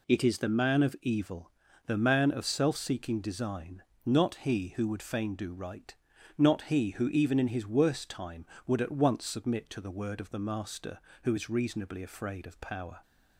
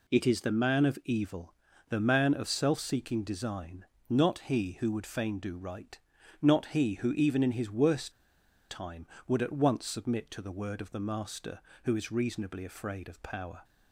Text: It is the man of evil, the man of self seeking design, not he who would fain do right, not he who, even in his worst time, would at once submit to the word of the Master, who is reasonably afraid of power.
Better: first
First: none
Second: pauses between "worst" and "time"; noticeable; at 8.1 s; 0.57 s long

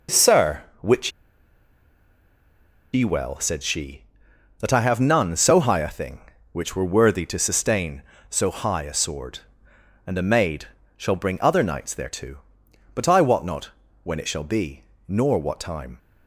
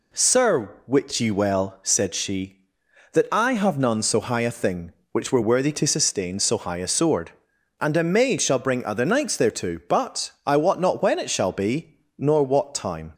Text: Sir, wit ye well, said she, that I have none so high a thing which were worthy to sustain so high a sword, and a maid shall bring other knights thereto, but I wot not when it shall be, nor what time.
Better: second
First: pauses between "wit" and "ye"; strong; at 1.1 s; 1.8 s long // pauses between "maid" and "shall"; slight; at 10.6 s; 0.28 s long // pauses between "not" and "when"; slight; at 13.7 s; 0.32 s long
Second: none

